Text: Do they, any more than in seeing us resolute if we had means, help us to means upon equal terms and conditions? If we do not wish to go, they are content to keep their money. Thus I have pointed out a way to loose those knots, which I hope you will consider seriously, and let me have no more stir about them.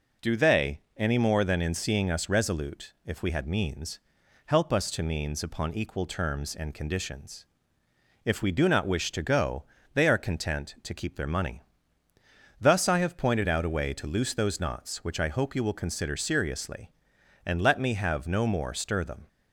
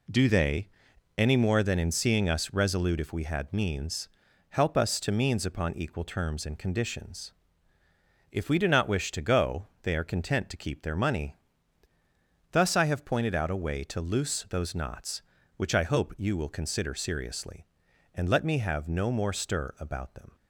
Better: second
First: skips "about"; at 19.0 s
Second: none

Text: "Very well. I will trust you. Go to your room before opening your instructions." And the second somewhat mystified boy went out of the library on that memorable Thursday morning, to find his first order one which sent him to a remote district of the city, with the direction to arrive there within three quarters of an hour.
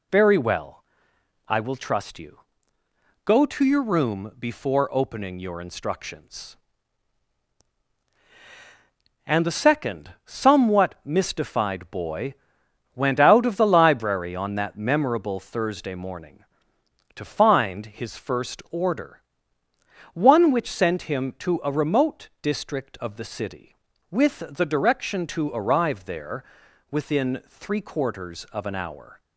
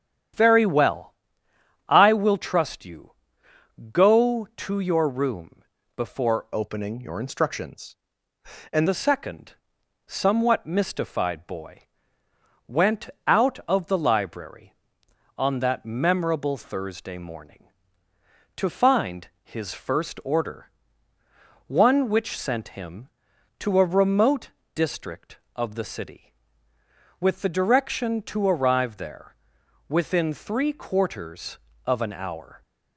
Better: first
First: pauses between "boy" and "went"; noticeable; at 12.3 s; 0.62 s long // pauses between "order" and "one"; noticeable; at 19.2 s; 0.92 s long // pauses between "there" and "within"; noticeable; at 26.4 s; 0.46 s long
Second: starts louder than the rest; strong; until 2.0 s; 9.5 dB // pauses between "room" and "before"; slight; at 5.6 s; 0.34 s long // changes voice from "opening" to "And"; from 6.5 to 8.8 s; 2.3 s long // pauses between "second" and "somewhat"; noticeable; at 9.5 s; 0.54 s long // pauses between "boy" and "went"; noticeable; at 11.8 s; 0.86 s long // pauses between "went" and "out"; slight; at 13.0 s; 0.18 s long // pauses between "order" and "one"; noticeable; at 20.6 s; 0.98 s long // pauses between "remote" and "district"; slight; at 24.4 s; 0.24 s long // pauses between "there" and "within"; noticeable; at 29.3 s; 0.52 s long

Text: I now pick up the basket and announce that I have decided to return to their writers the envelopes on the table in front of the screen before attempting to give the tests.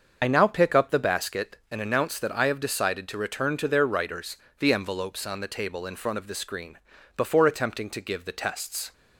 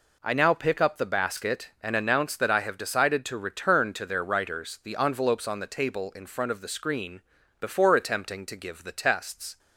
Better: second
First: loses the start of "I"; at 0.2 s; 45 ms // starts louder than the rest; until 1.2 s; 6.5 dB // pauses between "writers" and "the"; slight; at 4.3 s; 0.24 s long // pauses between "screen" and "before"; at 6.7 s; 0.38 s long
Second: pauses between "screen" and "before"; at 7.2 s; 0.40 s long

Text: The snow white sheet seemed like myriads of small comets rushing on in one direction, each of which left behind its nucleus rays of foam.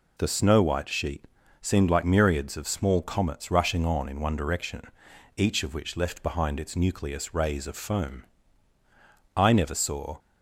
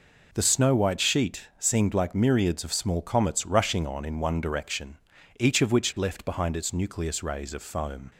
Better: second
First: pauses between "sheet" and "seemed"; slight; at 1.2 s; 0.36 s long // goes on to say "I never saw"; noticeable; from 9.3 s on; 0.84 s long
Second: none

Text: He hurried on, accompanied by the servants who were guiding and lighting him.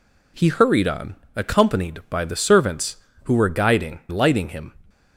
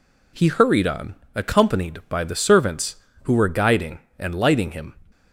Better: second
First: skips "and"; at 4.0 s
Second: none

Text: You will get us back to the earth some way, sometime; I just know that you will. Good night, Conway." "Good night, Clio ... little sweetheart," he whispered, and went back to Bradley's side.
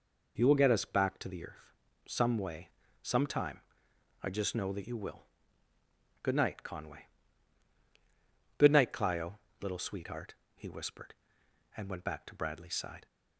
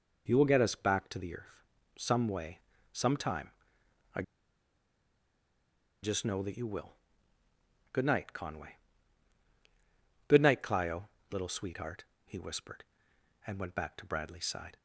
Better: first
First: pauses between "earth" and "some"; slight; at 1.7 s; 0.34 s long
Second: pauses between "earth" and "some"; slight; at 1.6 s; 0.34 s long // pauses between "I" and "just"; strong; at 4.2 s; 1.8 s long

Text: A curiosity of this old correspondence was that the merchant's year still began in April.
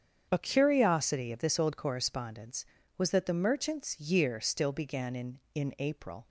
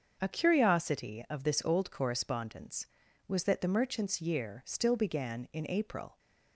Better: second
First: starts louder than the rest; strong; until 1.3 s; 7.5 dB // says "in" twice; at 5.5 s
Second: starts louder than the rest; until 1.2 s; 6.5 dB

